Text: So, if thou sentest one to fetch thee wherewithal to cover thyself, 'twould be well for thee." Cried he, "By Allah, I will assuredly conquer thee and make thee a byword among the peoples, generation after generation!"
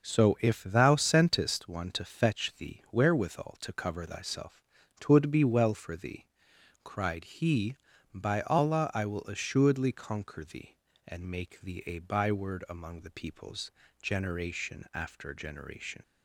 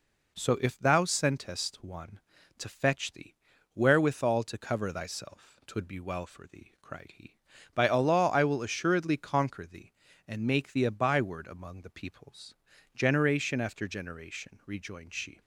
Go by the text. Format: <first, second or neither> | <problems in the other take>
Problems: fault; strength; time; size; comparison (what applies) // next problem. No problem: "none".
first | pauses between "thee" and "wherewithal"; at 3.3 s; 0.40 s long // goes on to say "Rejoined she"; noticeable; from 14.6 s on; 0.74 s long